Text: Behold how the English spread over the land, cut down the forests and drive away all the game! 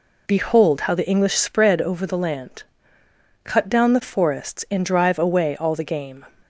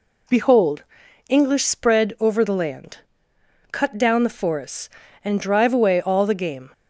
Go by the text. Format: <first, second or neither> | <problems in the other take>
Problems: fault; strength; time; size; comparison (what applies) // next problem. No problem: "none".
first | skips "how the"; at 1.0 s